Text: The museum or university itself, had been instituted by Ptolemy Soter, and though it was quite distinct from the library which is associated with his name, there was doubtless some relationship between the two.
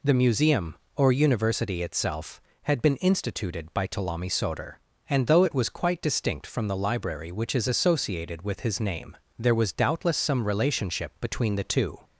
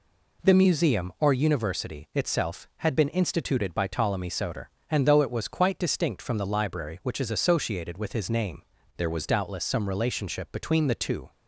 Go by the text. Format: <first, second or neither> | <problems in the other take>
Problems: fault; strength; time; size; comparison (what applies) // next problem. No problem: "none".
first | changes voice from "there" to "was"; from 8.9 to 9.2 s; 0.3 s long